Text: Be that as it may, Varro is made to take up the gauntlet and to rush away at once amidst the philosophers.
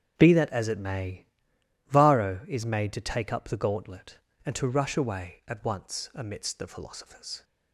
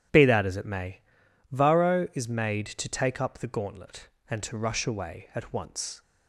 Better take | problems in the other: first | starts louder than the rest; strong; until 1.6 s; 10.5 dB; strong in the first // stops before "amidst the philosophers"; at 6.0 s

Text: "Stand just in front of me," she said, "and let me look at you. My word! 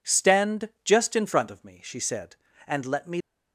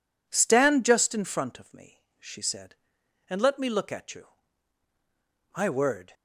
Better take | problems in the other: second | stops before "look at you My word"; at 3.2 s

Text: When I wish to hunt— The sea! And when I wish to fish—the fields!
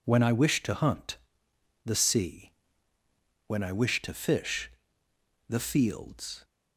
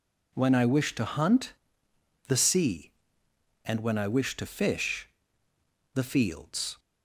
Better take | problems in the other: second | skips "And"; at 2.9 s

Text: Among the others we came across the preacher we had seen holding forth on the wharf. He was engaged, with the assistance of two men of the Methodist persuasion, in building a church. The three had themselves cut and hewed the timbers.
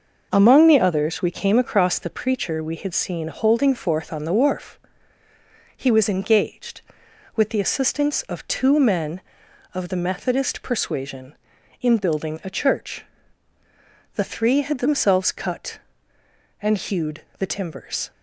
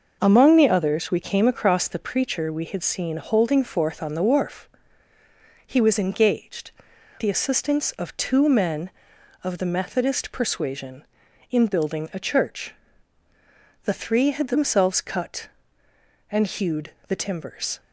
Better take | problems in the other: first | skips "with"; at 6.9 s // pauses between "hewed" and "the"; slight; at 16.9 s; 0.16 s long; slight in the first

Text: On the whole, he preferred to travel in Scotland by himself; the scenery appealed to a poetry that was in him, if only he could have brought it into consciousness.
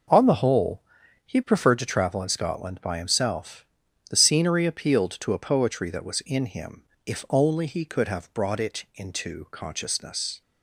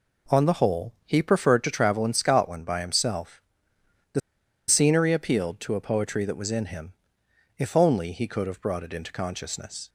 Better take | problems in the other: first | pauses between "the" and "scenery"; noticeable; at 4.1 s; 0.48 s long

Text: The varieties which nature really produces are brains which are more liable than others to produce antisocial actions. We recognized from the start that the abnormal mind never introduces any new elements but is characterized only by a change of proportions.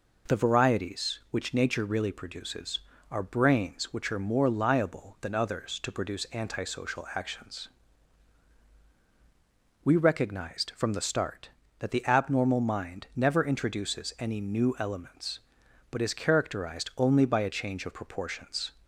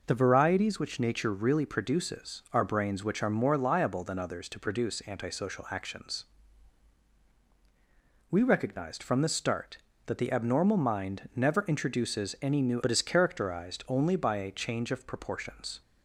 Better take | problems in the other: first | skips "elements"; at 12.8 s

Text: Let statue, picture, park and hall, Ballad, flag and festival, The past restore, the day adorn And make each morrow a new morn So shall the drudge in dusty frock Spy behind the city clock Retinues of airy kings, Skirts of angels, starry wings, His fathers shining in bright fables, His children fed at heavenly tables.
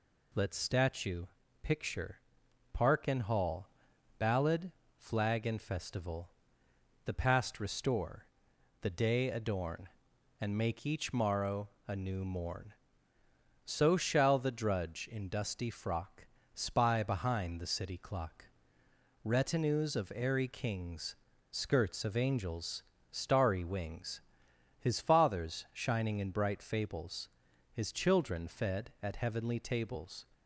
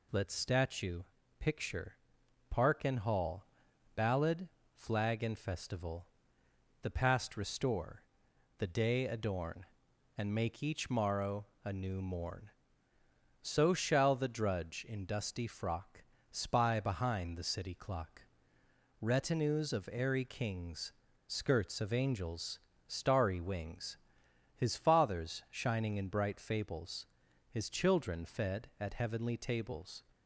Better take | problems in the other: neither | pauses between "morrow" and "a"; slight; the same in both // pauses between "frock" and "Spy"; slight; the same in both // pauses between "clock" and "Retinues"; noticeable; the same in both

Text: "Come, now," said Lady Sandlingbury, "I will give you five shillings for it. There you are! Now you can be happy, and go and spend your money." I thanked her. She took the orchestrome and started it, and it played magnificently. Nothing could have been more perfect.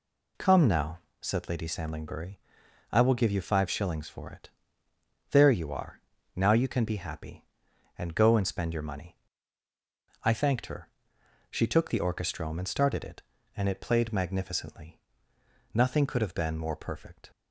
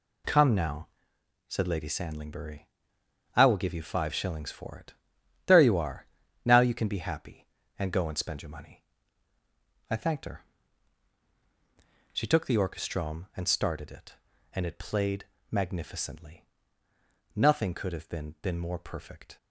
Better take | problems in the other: first | pauses between "played" and "magnificently"; slight; at 15.2 s; 0.26 s long // says "been" twice; at 18.4 s

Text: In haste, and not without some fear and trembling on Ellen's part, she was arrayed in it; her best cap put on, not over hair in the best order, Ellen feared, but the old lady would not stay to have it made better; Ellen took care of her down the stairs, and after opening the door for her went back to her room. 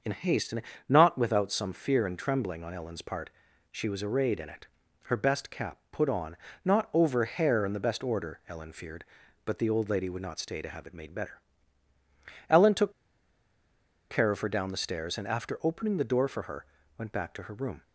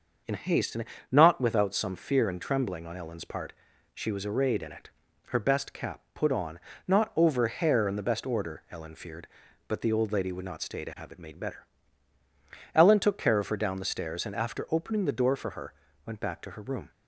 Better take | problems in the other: second | starts louder than the rest; until 1.3 s; 6.5 dB; also in the second // pauses between "and" and "not"; slight; at 0.6 s; 0.28 s long; slight in the second // pauses between "took" and "care"; at 12.9 s; 1.1 s long // pauses between "her" and "went"; slight; at 16.6 s; 0.32 s long; slight in the second

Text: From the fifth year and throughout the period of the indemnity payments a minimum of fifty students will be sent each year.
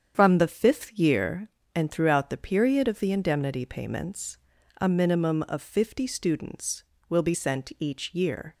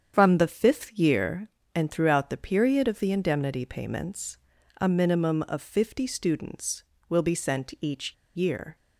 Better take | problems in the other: first | starts louder than the rest; strong; until 1.1 s; 8 dB; strong in the first // pauses between "payments" and "a"; at 4.3 s; 0.42 s long; also in the first // pauses between "each" and "year"; slight; at 8.1 s; 0.20 s long

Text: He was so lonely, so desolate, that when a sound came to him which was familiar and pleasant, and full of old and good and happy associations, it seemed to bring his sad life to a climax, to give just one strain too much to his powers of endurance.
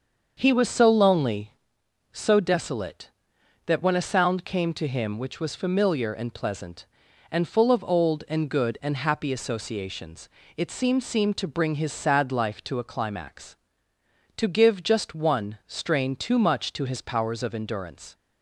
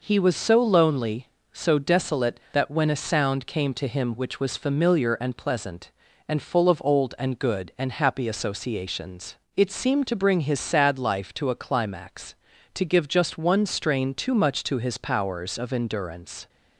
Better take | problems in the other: second | starts louder than the rest; until 1.3 s; 6.5 dB // says "seemed" twice; at 11.0 s

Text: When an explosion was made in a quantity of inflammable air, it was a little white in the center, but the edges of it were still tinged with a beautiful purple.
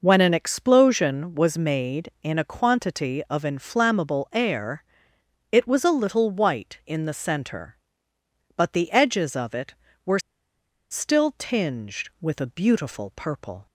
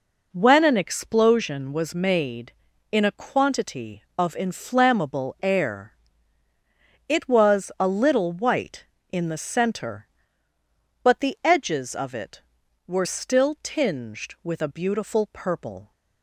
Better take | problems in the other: second | pauses between "were" and "still"; noticeable; at 10.1 s; 0.72 s long

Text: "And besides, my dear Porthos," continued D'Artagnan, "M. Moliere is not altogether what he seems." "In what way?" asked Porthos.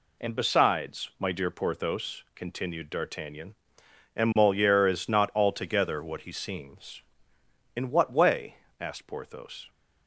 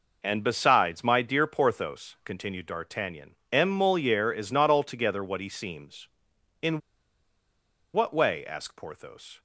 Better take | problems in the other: first | pauses between "In" and "what"; at 6.7 s; 1.1 s long

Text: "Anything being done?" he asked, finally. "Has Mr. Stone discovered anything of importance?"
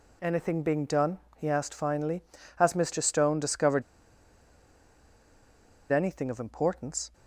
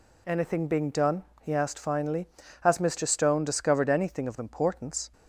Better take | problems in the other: second | pauses between "discovered" and "anything"; strong; at 3.8 s; 2.1 s long

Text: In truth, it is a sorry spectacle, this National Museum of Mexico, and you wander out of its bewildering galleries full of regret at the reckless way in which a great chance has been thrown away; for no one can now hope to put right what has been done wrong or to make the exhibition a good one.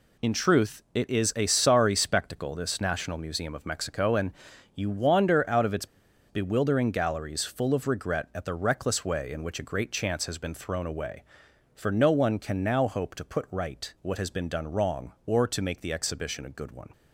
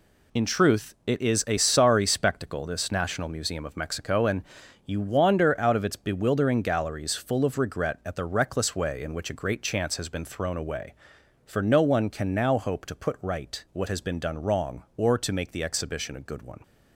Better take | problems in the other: second | pauses between "and" and "you"; at 4.3 s; 0.42 s long; also in the second // pauses between "its" and "bewildering"; at 5.8 s; 0.42 s long

